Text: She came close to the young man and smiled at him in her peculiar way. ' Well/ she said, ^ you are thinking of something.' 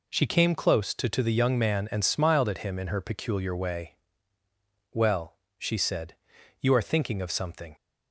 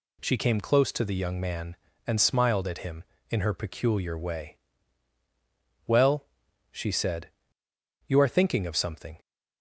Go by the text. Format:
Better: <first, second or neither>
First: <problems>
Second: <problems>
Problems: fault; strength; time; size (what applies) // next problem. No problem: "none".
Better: second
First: says "to" twice; at 1.0 s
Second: none